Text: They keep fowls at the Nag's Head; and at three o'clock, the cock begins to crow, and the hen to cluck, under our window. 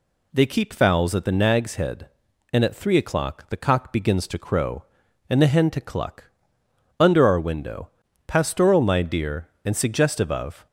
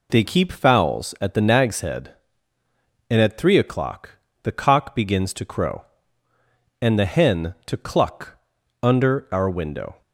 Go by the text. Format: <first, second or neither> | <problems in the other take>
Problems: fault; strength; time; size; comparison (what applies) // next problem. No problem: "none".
second | goes on to say "Pastoral my dear and suggestive of"; strong; from 8.2 s on; 2.4 s long